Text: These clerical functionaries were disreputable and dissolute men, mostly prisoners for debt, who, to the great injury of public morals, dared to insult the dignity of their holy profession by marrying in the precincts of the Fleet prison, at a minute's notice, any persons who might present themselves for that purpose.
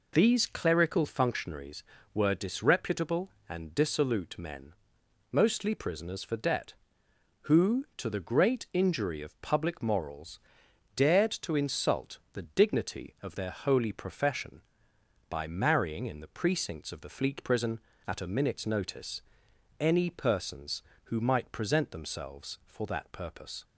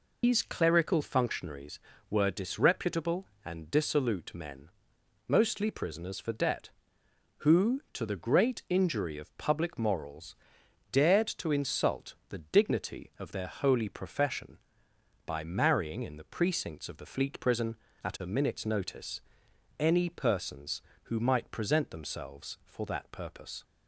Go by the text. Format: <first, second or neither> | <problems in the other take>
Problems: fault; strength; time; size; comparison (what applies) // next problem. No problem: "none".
first | loses the start of "These"; at 0.2 s; 145 ms